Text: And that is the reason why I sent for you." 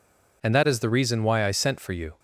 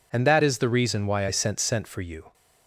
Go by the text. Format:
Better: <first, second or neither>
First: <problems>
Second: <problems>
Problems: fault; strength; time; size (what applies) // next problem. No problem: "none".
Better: first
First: none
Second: says "sent" twice; at 1.5 s